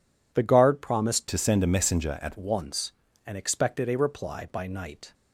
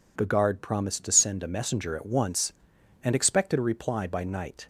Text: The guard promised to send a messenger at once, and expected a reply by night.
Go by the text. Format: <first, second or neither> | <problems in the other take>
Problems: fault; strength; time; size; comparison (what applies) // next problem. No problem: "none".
second | changes voice from "to" to "at"; from 1.2 to 2.3 s; 1.1 s long